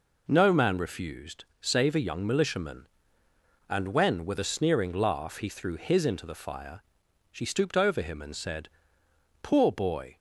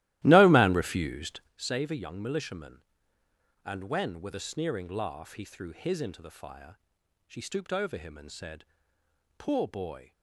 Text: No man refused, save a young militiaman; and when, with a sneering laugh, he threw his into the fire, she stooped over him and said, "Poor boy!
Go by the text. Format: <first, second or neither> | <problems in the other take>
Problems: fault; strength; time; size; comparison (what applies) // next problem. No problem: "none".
first | starts louder than the rest; strong; until 1.6 s; 15.5 dB